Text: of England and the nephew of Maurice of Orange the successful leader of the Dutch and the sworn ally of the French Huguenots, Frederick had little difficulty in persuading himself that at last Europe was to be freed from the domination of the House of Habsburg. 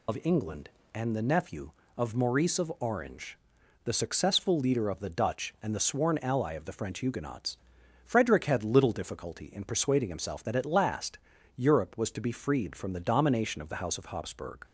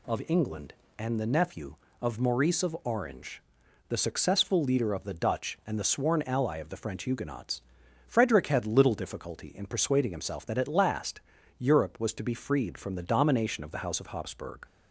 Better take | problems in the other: second | loses the start of "of"; at 0.0 s; 65 ms // pauses between "Orange" and "the"; noticeable; at 3.3 s; 0.46 s long; noticeable in the second // pauses between "last" and "Europe"; at 11.1 s; 0.38 s long; also in the second

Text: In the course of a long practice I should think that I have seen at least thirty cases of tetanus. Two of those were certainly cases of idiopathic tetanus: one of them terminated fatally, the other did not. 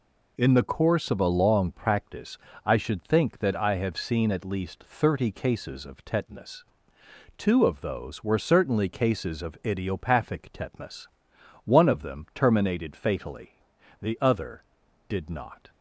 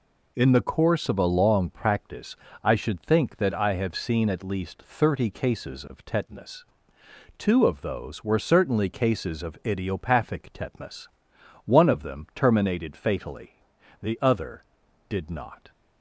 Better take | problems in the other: neither | pauses between "practice" and "I"; slight; the same in both

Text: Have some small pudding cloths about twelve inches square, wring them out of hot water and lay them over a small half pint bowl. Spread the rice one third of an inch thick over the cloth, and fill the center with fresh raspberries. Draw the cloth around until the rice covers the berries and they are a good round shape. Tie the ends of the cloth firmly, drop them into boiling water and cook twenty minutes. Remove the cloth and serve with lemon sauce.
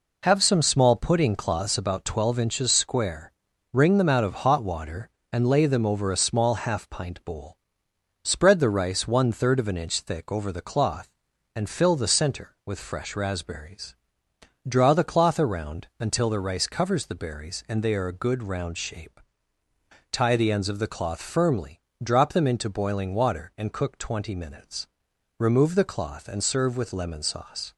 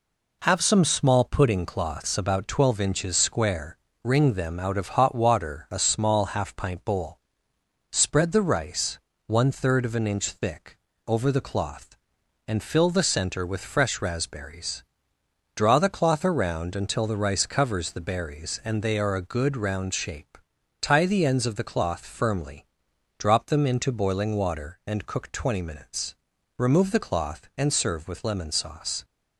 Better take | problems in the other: first | skips "and lay them over"; at 5.6 s // pauses between "rice" and "one"; slight; at 8.9 s; 0.28 s long // pauses between "thick" and "over"; slight; at 10.7 s; 0.28 s long

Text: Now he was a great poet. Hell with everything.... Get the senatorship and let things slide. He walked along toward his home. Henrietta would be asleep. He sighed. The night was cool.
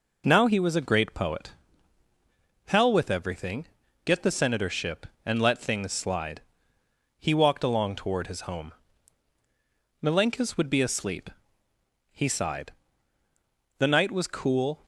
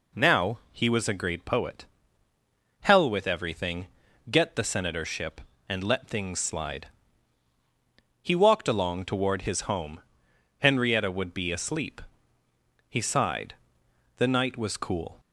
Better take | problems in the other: second | says "Milenkis" for "Henrietta"; at 10.0 s

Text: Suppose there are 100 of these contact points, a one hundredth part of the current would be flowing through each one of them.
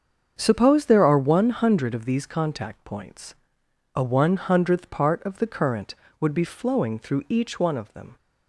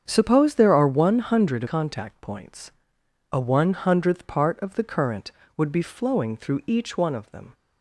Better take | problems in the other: first | starts louder than the rest; strong; until 1.0 s; 7.5 dB; also in the first // skips "of these"; at 1.6 s

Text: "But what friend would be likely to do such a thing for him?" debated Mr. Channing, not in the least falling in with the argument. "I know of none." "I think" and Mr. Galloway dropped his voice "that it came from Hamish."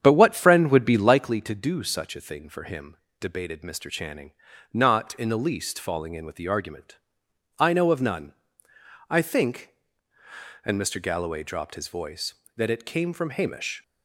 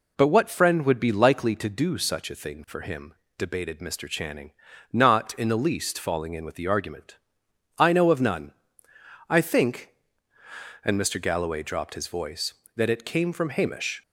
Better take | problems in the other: second | starts louder than the rest; strong; until 1.2 s; 8.5 dB

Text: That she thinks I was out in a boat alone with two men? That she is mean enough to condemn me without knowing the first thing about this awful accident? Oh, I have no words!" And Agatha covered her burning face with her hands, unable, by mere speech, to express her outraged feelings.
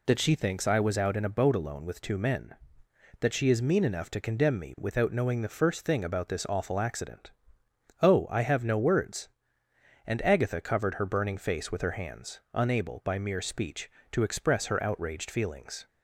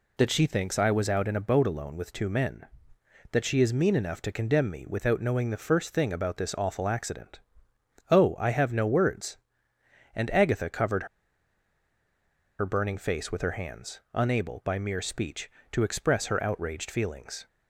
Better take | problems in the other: first | pauses between "covered" and "her"; strong; at 11.0 s; 1.5 s long

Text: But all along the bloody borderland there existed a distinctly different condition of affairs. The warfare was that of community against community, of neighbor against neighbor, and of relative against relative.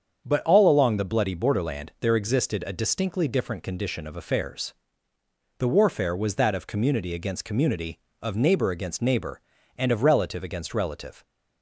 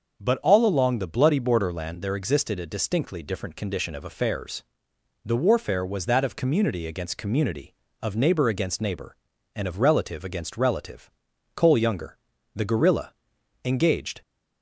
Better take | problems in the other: first | starts louder than the rest; until 1.2 s; 6.5 dB; strong in the first // goes on to say "Cole Younger the Guerrilla engaged"; strong; from 11.5 s on; 2.6 s long

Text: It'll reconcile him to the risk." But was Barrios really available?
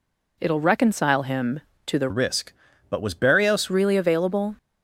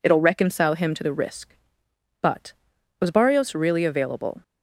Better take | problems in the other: second | changes voice from "risk" to "Barrios"; from 2.0 to 3.7 s; 1.7 s long

